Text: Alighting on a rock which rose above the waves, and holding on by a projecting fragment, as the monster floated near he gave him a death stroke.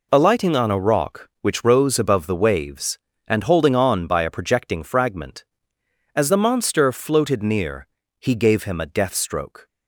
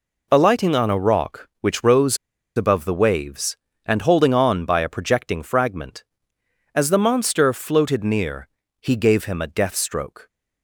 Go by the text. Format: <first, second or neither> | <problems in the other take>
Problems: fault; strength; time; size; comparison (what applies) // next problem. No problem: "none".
first | pauses between "rose" and "above"; at 2.1 s; 0.40 s long // pauses between "near" and "he"; slight; at 8.4 s; 0.32 s long; slight in the first